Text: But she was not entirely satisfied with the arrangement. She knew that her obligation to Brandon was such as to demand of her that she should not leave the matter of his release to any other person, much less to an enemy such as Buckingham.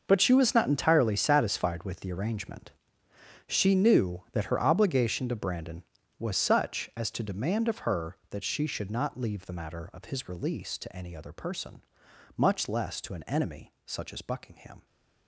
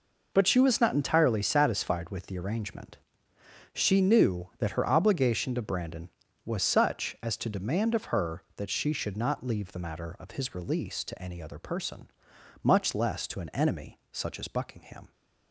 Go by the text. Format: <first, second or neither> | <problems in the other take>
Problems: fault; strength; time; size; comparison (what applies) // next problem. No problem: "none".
second | gets quieter; strong; throughout; 15 dB